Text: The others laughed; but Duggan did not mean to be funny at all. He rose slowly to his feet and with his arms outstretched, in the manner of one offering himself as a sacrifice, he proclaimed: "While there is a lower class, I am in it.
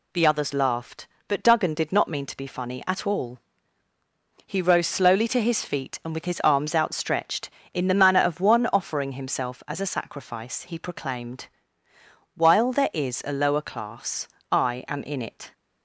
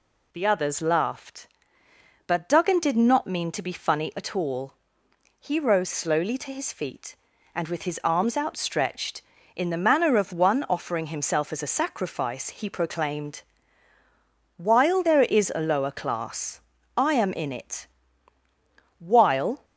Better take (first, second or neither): first